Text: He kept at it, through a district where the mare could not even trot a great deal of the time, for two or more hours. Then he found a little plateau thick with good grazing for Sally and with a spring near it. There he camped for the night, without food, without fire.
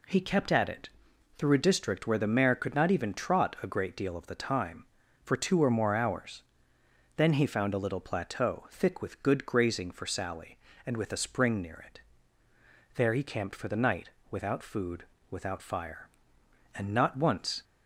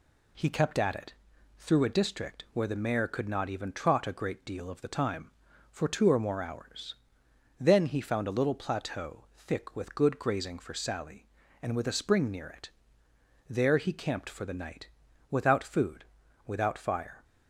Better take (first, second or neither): second